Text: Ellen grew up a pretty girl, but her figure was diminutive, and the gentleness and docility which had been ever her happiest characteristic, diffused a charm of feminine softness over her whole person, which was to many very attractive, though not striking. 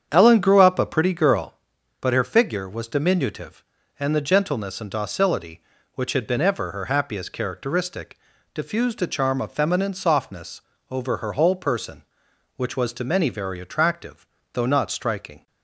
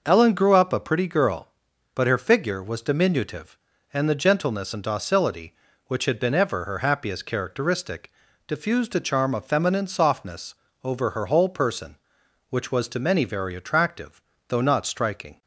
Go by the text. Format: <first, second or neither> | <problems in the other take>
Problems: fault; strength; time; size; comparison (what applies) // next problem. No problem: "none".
second | starts louder than the rest; strong; until 1.7 s; 8 dB // pauses between "softness" and "over"; slight; at 10.6 s; 0.30 s long; slight in the second